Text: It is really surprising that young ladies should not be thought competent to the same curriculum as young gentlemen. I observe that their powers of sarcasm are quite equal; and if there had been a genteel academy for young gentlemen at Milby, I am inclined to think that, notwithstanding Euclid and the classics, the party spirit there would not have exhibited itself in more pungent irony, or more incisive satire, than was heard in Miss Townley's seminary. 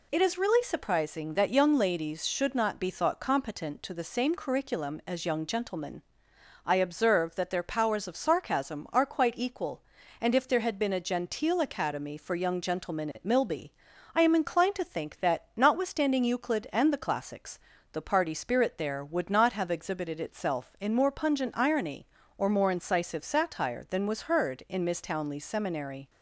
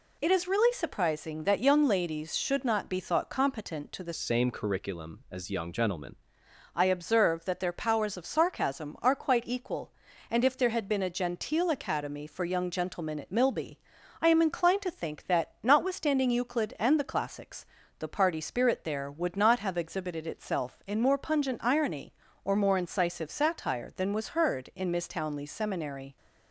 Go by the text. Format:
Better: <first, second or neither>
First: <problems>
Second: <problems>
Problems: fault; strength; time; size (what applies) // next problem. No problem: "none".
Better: first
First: none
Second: changes voice from "same" to "gentlemen"; from 4.1 to 6.1 s; 2.0 s long